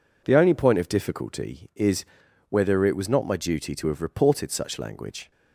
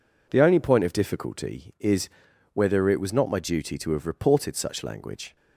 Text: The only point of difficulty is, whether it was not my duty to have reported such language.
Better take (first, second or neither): neither